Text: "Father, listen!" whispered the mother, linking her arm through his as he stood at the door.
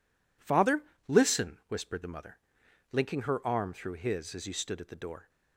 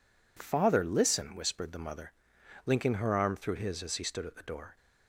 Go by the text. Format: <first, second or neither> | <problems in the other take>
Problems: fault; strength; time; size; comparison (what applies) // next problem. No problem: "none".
neither | none